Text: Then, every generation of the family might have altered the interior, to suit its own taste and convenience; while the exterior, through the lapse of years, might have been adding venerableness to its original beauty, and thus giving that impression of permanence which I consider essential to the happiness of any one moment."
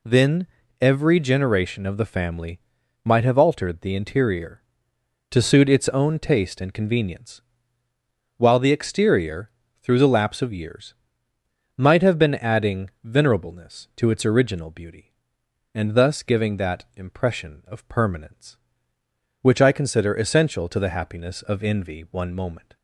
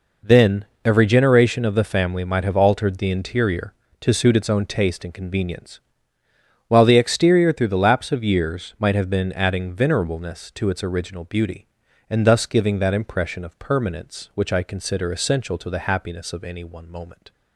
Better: second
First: pauses between "family" and "might"; at 2.6 s; 0.44 s long // pauses between "adding" and "venerableness"; slight; at 12.9 s; 0.16 s long // says "envy" for "any"; at 21.6 s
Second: none

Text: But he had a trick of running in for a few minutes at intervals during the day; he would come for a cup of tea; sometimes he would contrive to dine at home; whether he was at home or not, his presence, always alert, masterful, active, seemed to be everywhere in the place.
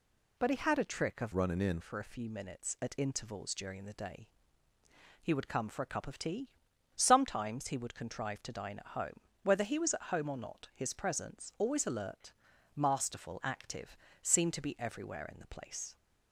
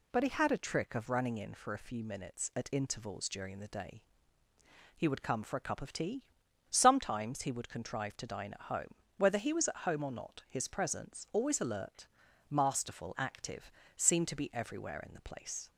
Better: second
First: changes voice from "running" to "in"; from 1.3 to 1.7 s; 0.4 s long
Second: none

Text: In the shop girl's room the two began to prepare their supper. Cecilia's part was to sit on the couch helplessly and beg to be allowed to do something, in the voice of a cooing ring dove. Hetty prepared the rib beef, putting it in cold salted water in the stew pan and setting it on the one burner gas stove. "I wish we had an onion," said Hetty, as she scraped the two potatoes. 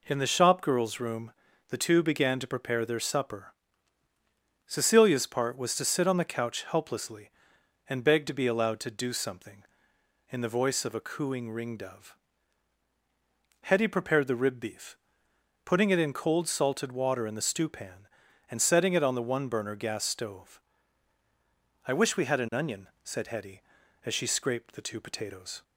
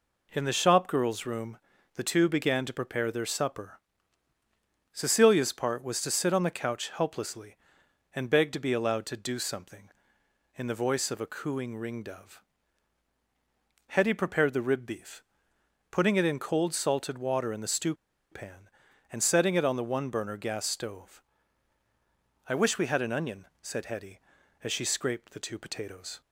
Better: first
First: pauses between "room" and "the"; at 1.3 s; 0.38 s long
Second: pauses between "room" and "the"; at 1.5 s; 0.38 s long // pauses between "stew" and "pan"; at 17.9 s; 0.36 s long

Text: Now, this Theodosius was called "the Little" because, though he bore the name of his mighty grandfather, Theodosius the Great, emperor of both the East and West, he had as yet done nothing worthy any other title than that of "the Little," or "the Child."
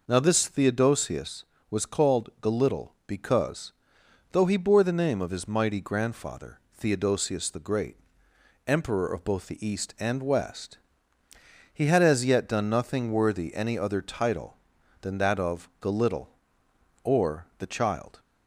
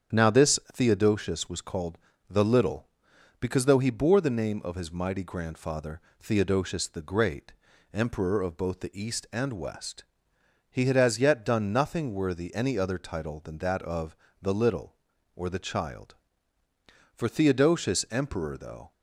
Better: first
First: none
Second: starts louder than the rest; strong; until 1.2 s; 8 dB // pauses between "called" and "the"; slight; at 1.9 s; 0.32 s long // pauses between "of" and "the"; slight; at 14.1 s; 0.24 s long // goes on to say "For Theodosius emperor though"; strong; from 17.1 s on; 1.7 s long

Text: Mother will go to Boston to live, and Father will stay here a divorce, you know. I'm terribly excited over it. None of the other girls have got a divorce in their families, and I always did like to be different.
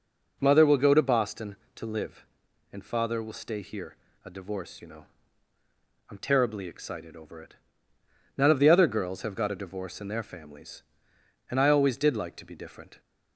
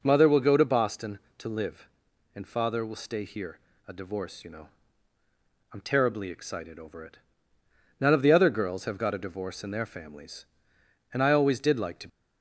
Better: first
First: pauses between "here" and "a"; slight; at 3.9 s; 0.28 s long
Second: pauses between "here" and "a"; slight; at 3.5 s; 0.28 s long // stops before "be different"; at 12.0 s

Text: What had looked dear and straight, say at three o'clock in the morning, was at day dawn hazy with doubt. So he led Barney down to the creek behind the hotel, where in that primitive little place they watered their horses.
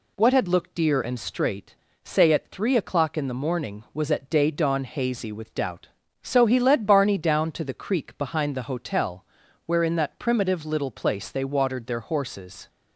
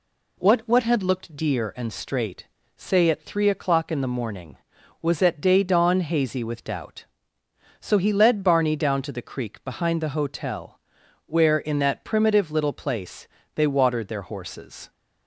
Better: first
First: none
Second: says "What" twice; at 0.6 s // pauses between "place" and "they"; slight; at 13.2 s; 0.30 s long

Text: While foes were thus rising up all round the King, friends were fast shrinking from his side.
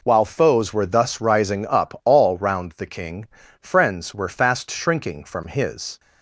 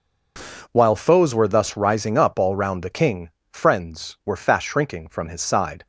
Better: second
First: stops before "side"; at 5.9 s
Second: none

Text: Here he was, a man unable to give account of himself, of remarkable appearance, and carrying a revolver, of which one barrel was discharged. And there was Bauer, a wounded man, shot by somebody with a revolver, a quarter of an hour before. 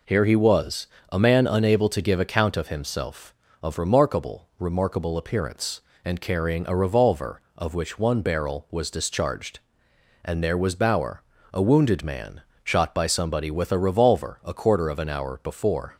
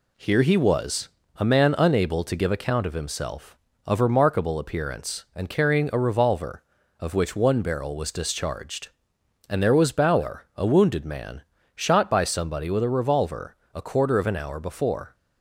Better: second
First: says "remarkable" twice; at 4.5 s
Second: none

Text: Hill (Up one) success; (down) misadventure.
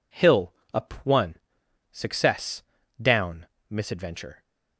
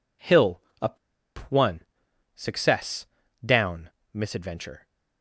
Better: first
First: none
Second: pauses between "Up" and "one"; noticeable; at 0.9 s; 0.51 s long

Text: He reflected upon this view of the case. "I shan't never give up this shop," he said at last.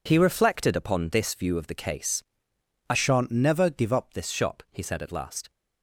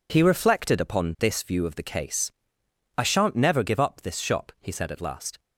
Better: second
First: changes voice from "shan't" to "up"; from 2.9 to 4.1 s; 1.2 s long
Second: none

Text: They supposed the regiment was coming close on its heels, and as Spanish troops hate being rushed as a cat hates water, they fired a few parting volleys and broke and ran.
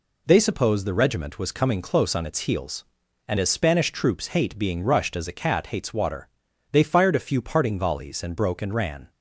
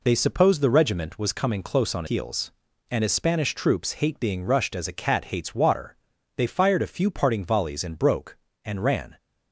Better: first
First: none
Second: skips "its"; at 2.0 s

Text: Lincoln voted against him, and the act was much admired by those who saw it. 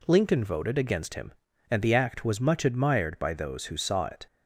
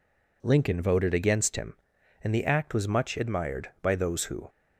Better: first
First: none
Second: stops before "saw it"; at 4.4 s

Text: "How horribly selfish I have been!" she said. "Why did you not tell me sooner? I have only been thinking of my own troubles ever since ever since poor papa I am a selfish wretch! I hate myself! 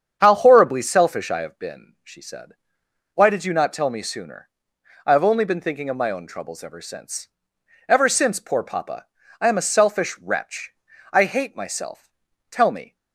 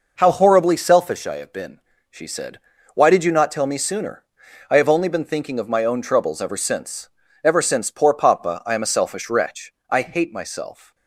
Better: second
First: starts louder than the rest; strong; until 1.2 s; 7.5 dB // pauses between "since" and "ever"; noticeable; at 7.2 s; 0.58 s long // pauses between "papa" and "I"; slight; at 9.0 s; 0.34 s long // goes on to say "Tell me"; slight; from 12.4 s on; 0.46 s long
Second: pauses between "since" and "ever"; slight; at 7.0 s; 0.36 s long

